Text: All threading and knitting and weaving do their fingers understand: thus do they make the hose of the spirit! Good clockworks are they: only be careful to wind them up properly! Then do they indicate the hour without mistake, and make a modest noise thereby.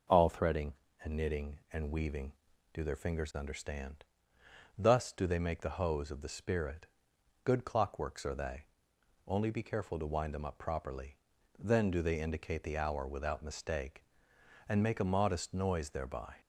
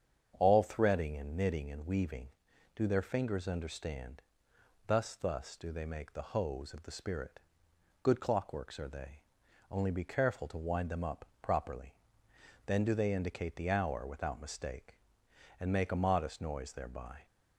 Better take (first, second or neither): first